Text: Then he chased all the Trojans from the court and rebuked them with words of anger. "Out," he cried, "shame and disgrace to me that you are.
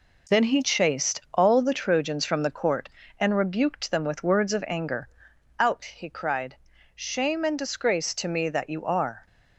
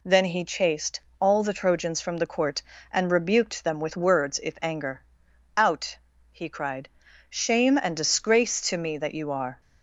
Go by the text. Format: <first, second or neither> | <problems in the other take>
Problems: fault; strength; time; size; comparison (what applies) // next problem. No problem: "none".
first | pauses between "chased" and "all"; slight; at 0.9 s; 0.20 s long // says "if" for "of"; at 4.4 s